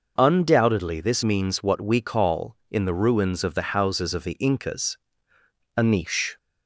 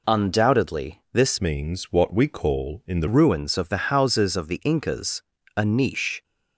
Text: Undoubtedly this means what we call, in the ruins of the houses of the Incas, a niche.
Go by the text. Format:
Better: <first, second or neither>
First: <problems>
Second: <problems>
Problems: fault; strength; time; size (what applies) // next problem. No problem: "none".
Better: first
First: none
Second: changes voice from "means" to "the"; from 1.4 to 3.0 s; 1.6 s long